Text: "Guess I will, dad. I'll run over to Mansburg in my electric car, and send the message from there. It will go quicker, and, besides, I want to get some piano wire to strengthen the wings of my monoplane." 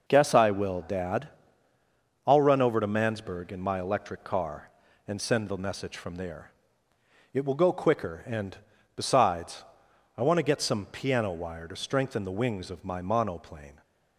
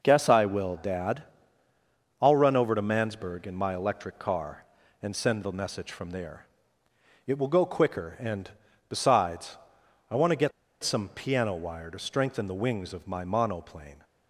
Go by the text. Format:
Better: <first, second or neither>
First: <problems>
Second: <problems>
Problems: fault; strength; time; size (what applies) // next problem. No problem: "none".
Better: first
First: none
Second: pauses between "get" and "some"; slight; at 10.5 s; 0.32 s long